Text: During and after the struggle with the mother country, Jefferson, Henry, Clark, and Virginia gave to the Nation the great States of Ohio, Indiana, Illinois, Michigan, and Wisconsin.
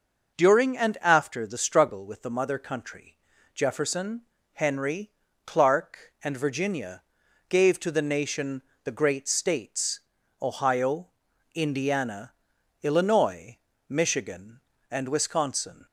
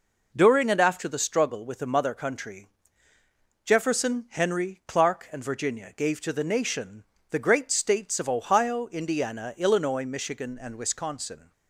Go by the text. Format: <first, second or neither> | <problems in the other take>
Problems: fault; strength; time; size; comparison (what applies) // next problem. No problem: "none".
second | pauses between "Virginia" and "gave"; noticeable; at 7.0 s; 0.46 s long // pauses between "Nation" and "the"; slight; at 8.6 s; 0.22 s long; slight in the second // skips "of"; at 10.2 s